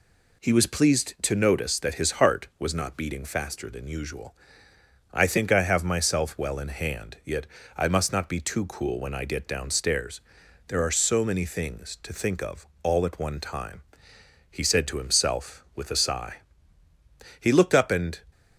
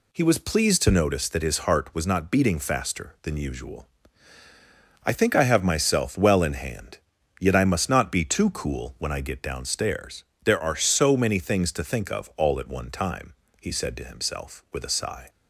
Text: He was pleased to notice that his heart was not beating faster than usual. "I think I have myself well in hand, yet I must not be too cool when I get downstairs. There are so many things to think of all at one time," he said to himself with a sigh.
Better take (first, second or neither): second